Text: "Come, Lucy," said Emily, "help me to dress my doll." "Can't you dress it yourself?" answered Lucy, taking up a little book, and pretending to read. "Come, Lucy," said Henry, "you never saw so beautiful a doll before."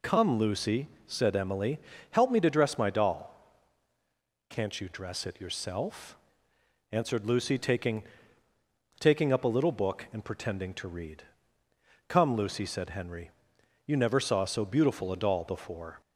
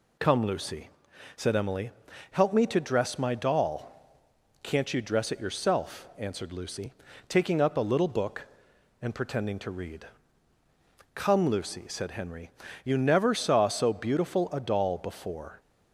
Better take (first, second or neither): second